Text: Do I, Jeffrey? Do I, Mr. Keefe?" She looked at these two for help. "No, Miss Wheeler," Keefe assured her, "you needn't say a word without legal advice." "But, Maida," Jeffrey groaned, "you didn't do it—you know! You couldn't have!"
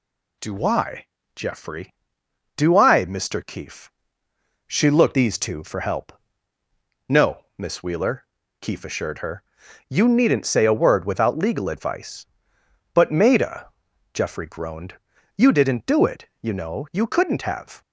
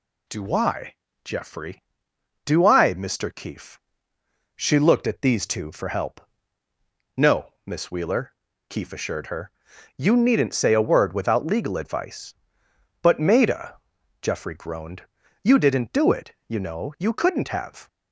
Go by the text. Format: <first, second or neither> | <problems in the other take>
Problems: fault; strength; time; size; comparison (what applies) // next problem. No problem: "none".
second | skips "at"; at 5.1 s